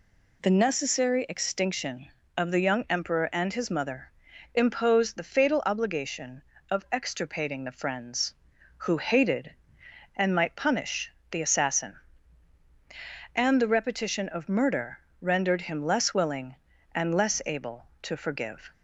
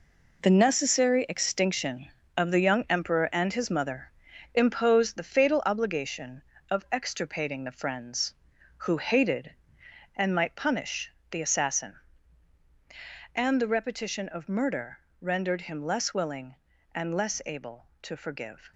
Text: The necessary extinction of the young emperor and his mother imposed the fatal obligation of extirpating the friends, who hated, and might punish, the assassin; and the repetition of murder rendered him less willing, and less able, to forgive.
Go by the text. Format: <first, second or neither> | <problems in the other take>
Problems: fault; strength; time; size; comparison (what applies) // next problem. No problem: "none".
first | gets quieter; strong; throughout; 10 dB // pauses between "mother" and "imposed"; at 4.0 s; 0.44 s long; also in the first // pauses between "murder" and "rendered"; slight; at 14.9 s; 0.20 s long; slight in the first